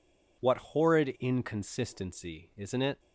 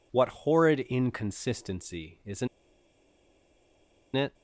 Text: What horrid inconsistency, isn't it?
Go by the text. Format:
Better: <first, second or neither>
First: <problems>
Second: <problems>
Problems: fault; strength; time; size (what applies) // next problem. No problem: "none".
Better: first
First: none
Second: pauses between "isn't" and "it"; strong; at 2.4 s; 1.6 s long